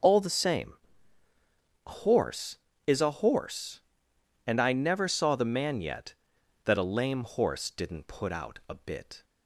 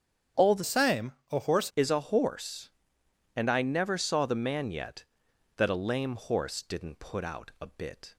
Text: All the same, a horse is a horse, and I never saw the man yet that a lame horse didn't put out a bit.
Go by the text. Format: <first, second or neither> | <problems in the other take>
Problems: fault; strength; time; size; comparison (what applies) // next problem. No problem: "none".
first | starts louder than the rest; strong; until 1.5 s; 8.5 dB // changes voice from "same" to "horse"; from 0.6 to 1.6 s; 1.0 s long